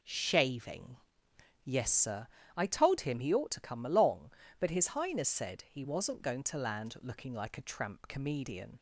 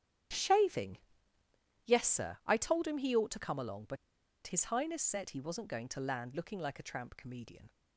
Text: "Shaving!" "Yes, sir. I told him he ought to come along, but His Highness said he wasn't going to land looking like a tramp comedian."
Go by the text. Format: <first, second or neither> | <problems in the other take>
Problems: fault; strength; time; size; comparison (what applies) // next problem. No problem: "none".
first | starts louder than the rest; strong; until 2.2 s; 11 dB // pauses between "but" and "His"; noticeable; at 3.9 s; 0.50 s long